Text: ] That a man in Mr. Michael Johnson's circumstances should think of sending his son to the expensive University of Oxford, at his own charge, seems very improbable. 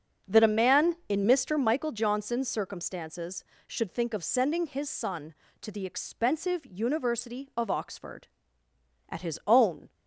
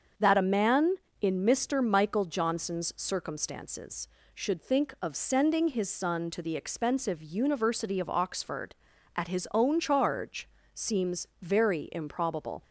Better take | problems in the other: second | starts louder than the rest; until 1.4 s; 6.5 dB; also in the second // stops before "charge seems very improbable"; at 9.9 s

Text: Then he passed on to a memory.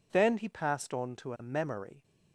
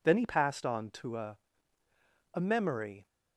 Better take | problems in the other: first | says "a" twice; at 2.3 s

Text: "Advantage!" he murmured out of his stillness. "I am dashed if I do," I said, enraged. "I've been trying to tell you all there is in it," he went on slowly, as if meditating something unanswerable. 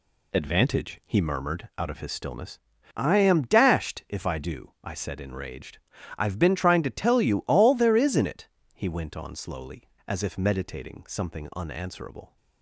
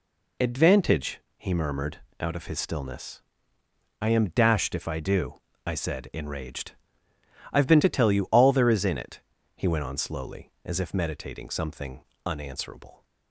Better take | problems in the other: first | pauses between "murmured" and "out"; slight; at 1.9 s; 0.20 s long // skips "trying"; at 7.8 s // pauses between "something" and "unanswerable"; slight; at 12.0 s; 0.22 s long

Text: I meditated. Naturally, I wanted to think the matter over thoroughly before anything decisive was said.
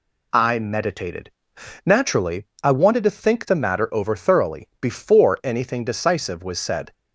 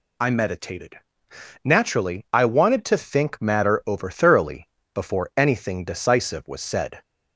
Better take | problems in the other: first | skips "the"; at 3.4 s // pauses between "thoroughly" and "before"; slight; at 4.6 s; 0.24 s long

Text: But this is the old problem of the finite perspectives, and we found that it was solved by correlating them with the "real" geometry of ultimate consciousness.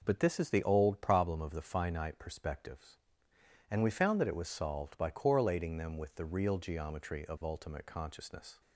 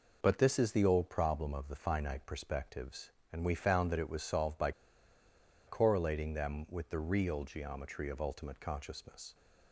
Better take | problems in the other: first | pauses between "by" and "correlating"; noticeable; at 4.7 s; 0.96 s long

